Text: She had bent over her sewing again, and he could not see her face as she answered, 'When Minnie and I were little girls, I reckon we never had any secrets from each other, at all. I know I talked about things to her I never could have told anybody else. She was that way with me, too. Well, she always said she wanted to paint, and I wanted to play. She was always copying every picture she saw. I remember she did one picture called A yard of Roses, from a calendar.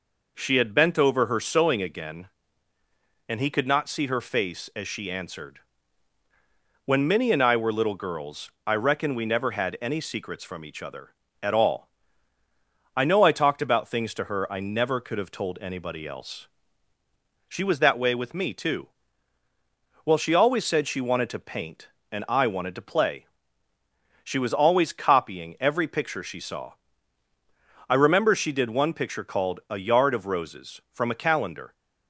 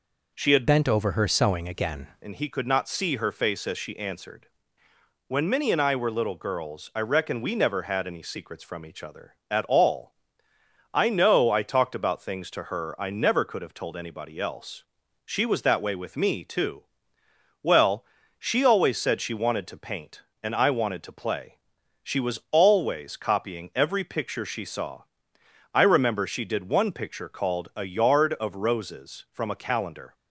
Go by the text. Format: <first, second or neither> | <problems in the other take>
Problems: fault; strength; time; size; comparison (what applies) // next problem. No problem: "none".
first | changes voice from "bent" to "again"; from 0.6 to 2.0 s; 1.4 s long